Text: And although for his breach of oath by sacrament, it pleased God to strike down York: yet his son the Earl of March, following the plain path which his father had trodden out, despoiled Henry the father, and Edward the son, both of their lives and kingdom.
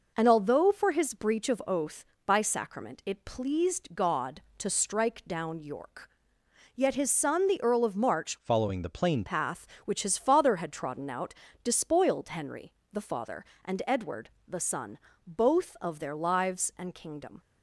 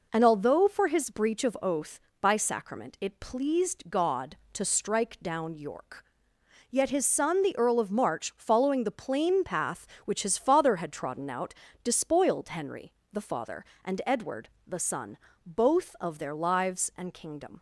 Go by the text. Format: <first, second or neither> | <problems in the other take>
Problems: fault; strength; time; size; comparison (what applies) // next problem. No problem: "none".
second | changes voice from "following" to "plain"; from 8.4 to 9.2 s; 0.8 s long // pauses between "Henry" and "the"; slight; at 12.7 s; 0.18 s long; slight in the second // pauses between "Edward" and "the"; slight; at 14.2 s; 0.18 s long; slight in the second